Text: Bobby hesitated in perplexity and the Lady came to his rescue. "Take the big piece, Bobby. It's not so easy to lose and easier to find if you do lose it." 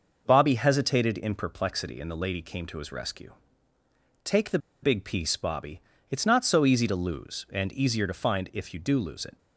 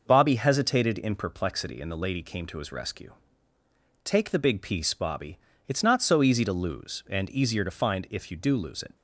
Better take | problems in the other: second | pauses between "the" and "big"; slight; at 4.5 s; 0.24 s long

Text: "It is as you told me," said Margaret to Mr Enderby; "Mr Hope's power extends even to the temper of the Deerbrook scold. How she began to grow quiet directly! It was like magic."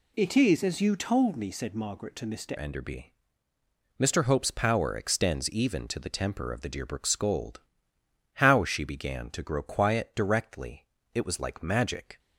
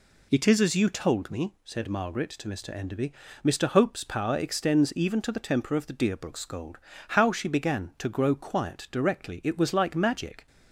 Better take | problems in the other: second | changes voice at "Enderby"; from 2.5 s on; 9.6 s long

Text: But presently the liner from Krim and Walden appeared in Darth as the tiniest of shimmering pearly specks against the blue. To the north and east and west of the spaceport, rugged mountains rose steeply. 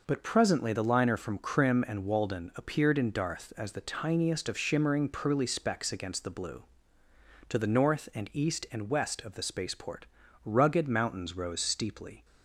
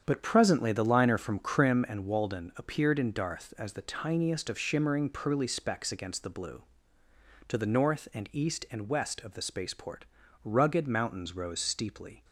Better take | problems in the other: first | starts louder than the rest; strong; until 1.9 s; 8 dB

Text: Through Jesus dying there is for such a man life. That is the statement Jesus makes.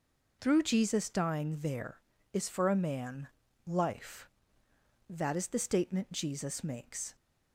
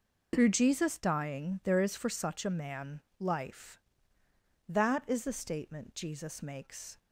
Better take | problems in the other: second | skips "such"; at 2.6 s // pauses between "man" and "life"; at 3.2 s; 0.38 s long; slight in the second

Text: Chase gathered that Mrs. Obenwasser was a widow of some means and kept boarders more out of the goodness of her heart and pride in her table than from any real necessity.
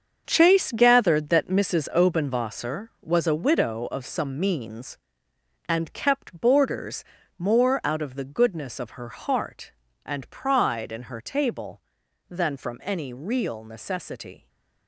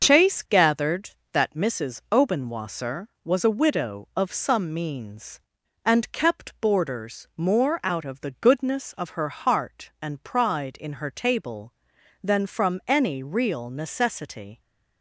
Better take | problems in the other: second | gets quieter; strong; throughout; 10 dB // starts louder than the rest; until 1.2 s; 6.5 dB; also in the second // pauses between "boarders" and "more"; slight; at 7.0 s; 0.34 s long

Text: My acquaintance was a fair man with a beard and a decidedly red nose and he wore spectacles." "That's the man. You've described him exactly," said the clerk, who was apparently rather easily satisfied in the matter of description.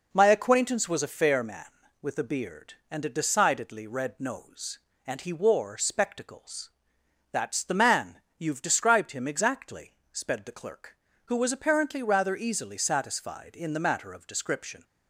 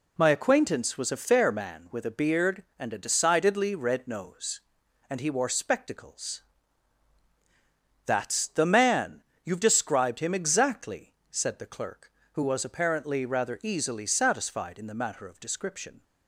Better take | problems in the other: second | says "sped" for "said"; at 10.1 s

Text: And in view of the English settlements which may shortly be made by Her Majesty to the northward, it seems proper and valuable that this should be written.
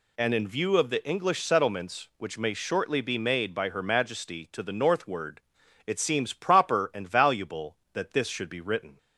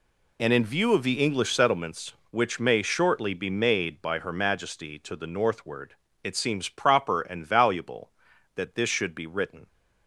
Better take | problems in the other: neither | none

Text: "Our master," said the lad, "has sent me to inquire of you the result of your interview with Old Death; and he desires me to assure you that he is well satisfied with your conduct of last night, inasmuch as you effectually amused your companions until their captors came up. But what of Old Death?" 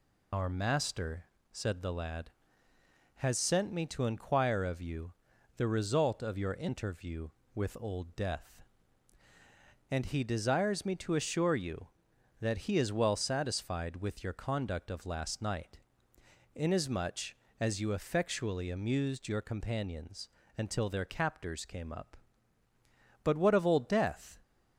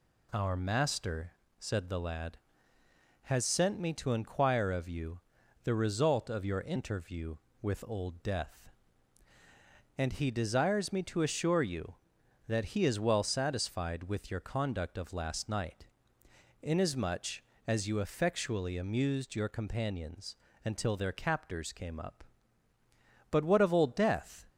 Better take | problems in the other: second | loses the start of "Our"; at 0.3 s; 110 ms // pauses between "you" and "the"; at 5.1 s; 0.44 s long; also in the second // pauses between "companions" and "until"; slight; at 20.2 s; 0.28 s long; slight in the second

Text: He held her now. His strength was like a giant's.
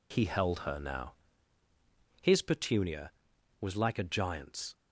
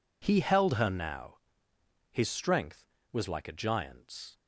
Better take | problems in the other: second | says "petunia" for "strength"; at 2.4 s

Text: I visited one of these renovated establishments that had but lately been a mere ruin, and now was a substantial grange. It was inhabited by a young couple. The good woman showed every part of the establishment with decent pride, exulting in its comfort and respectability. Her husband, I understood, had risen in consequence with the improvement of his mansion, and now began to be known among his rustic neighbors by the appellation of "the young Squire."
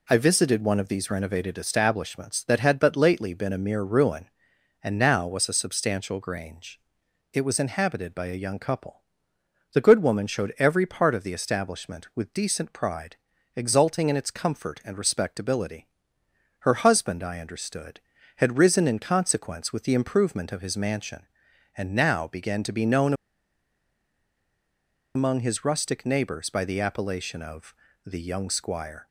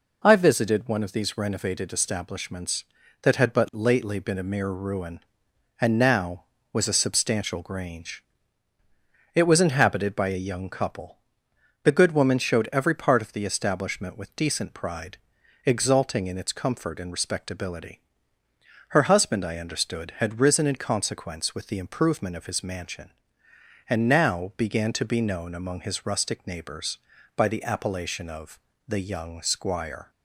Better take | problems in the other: second | pauses between "known" and "among"; strong; at 23.1 s; 2.0 s long // pauses between "of" and "the"; slight; at 27.7 s; 0.32 s long; slight in the second

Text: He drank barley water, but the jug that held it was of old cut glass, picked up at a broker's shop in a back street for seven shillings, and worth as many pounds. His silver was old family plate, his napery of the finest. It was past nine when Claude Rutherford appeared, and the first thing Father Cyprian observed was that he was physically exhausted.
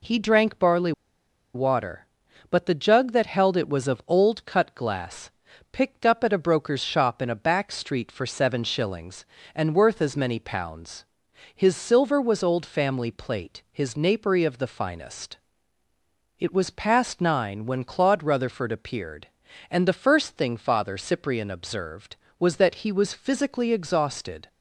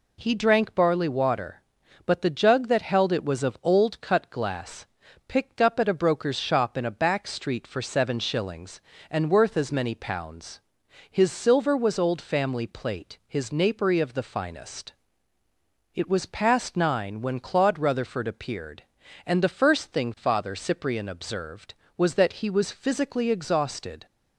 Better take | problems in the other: second | pauses between "barley" and "water"; noticeable; at 0.9 s; 0.63 s long

